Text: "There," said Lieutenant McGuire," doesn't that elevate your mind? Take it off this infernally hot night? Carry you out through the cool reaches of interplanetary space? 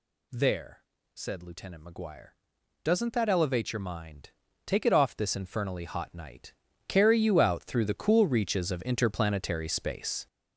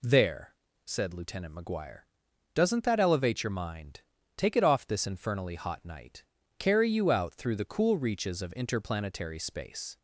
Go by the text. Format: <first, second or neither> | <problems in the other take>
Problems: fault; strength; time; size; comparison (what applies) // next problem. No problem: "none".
second | gets louder; strong; throughout; 7.5 dB